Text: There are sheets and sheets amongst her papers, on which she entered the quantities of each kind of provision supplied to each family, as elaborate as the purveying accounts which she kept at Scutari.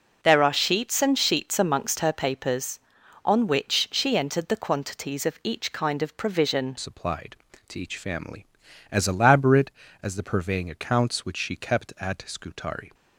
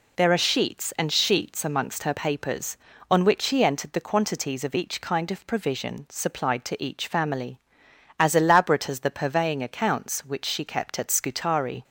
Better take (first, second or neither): second